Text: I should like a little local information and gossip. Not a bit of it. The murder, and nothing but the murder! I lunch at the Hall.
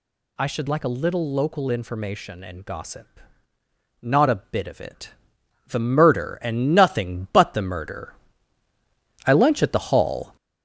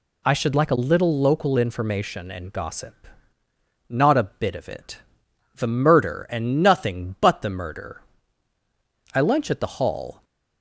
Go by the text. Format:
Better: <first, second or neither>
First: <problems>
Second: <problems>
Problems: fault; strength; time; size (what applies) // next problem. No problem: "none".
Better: second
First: gets louder; noticeable; throughout; 5.5 dB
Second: none